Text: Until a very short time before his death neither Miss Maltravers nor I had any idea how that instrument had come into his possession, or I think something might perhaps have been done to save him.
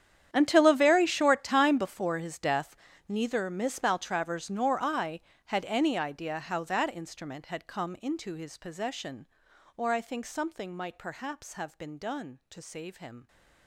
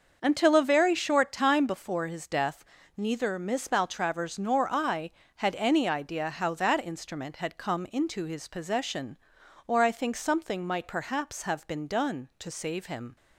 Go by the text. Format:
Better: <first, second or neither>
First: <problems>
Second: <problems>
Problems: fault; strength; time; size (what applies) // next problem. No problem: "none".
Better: second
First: gets quieter; strong; throughout; 18 dB // starts louder than the rest; strong; until 1.3 s; 9.5 dB // pauses between "death" and "neither"; slight; at 2.7 s; 0.32 s long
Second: starts louder than the rest; until 1.2 s; 6.5 dB // pauses between "death" and "neither"; slight; at 2.6 s; 0.32 s long